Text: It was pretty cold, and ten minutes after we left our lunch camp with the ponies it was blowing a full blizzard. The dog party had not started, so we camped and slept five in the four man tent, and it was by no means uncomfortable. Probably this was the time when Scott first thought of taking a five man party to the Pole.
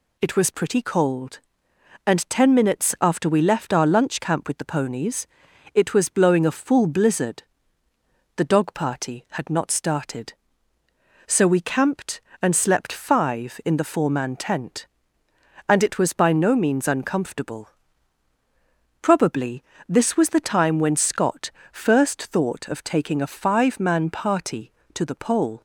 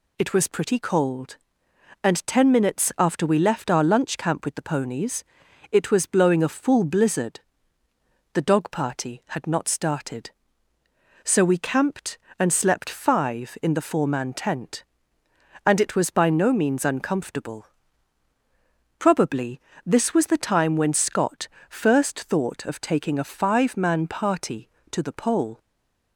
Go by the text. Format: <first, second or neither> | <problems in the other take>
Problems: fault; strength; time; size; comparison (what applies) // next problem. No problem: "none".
first | pauses between "ponies" and "it"; noticeable; at 5.2 s; 0.48 s long; noticeable in the first // pauses between "Probably" and "this"; slight; at 19.5 s; 0.26 s long; slight in the first // pauses between "Scott" and "first"; slight; at 21.4 s; 0.20 s long; slight in the first // stays silent after the last word; slight; from 25.5 s on; 0.6 s long